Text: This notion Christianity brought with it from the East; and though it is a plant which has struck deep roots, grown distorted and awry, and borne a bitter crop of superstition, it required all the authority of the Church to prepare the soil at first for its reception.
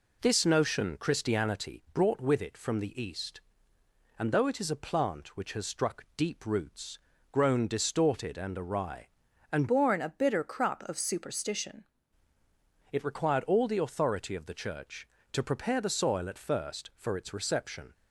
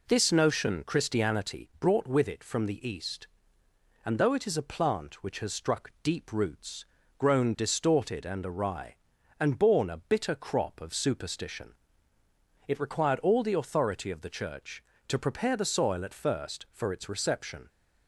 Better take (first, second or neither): second